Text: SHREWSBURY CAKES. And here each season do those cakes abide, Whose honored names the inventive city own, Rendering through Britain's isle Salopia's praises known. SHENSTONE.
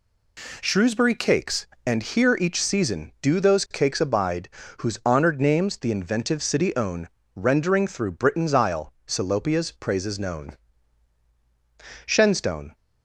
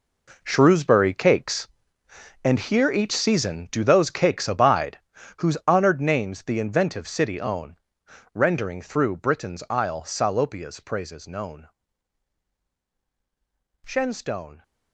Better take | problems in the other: first | gets quieter; strong; throughout; 12.5 dB

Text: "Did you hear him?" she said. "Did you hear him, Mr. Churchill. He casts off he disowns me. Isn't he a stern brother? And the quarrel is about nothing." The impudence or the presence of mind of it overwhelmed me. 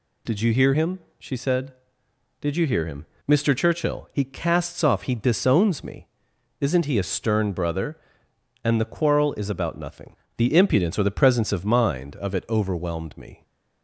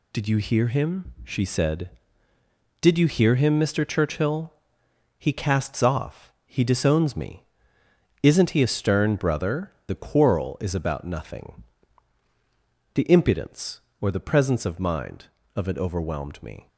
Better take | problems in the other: first | skips "And"; at 9.7 s

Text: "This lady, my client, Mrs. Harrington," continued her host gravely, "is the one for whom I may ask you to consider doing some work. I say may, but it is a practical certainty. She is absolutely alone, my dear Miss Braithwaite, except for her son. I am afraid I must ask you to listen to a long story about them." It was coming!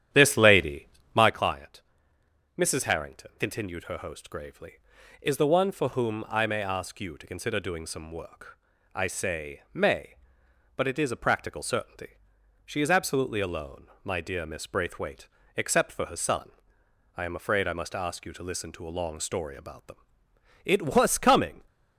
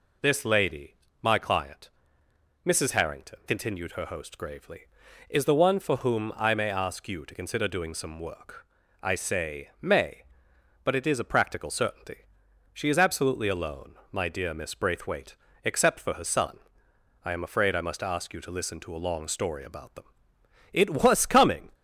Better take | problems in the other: second | starts louder than the rest; strong; until 1.5 s; 10.5 dB

